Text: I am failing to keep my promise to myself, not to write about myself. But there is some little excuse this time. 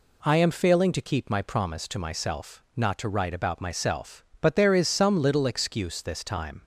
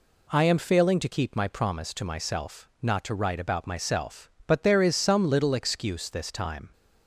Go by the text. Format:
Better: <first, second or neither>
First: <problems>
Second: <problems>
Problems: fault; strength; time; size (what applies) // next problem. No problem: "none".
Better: neither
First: none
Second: none